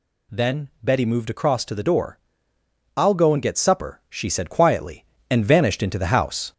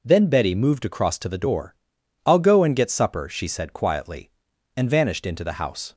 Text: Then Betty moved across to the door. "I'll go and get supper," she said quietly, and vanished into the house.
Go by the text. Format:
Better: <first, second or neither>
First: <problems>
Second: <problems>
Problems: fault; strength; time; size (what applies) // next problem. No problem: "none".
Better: second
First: gets louder; slight; throughout; 3 dB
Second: none